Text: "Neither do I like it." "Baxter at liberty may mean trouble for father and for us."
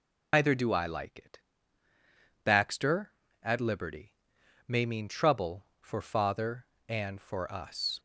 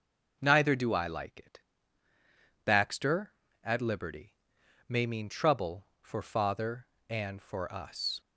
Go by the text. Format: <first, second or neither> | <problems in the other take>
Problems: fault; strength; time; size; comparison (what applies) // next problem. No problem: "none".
second | loses the start of "Neither"; at 0.3 s; 140 ms // pauses between "liberty" and "may"; noticeable; at 4.1 s; 0.52 s long; noticeable in the second